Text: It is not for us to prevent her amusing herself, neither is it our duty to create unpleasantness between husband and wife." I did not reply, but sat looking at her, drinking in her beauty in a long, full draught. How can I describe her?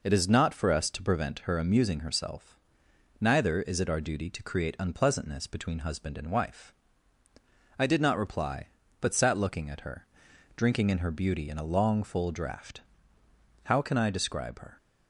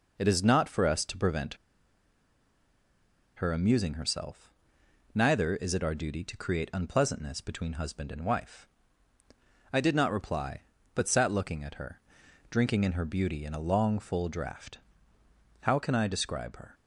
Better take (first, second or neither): first